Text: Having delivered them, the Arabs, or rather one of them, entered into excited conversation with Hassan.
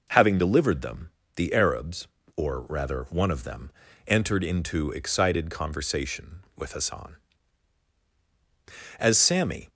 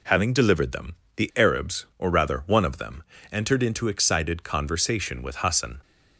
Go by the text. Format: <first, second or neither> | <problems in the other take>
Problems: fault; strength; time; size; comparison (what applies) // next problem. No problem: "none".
second | goes on to say "As Sammy"; noticeable; from 8.9 s on; 0.70 s long